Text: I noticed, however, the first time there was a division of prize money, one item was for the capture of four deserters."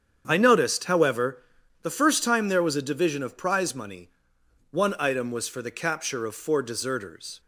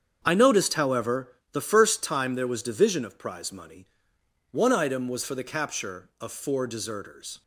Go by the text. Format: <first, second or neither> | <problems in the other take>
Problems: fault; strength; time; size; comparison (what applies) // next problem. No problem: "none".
first | starts louder than the rest; strong; until 1.2 s; 7.5 dB; strong in the first // skips "a"; at 2.6 s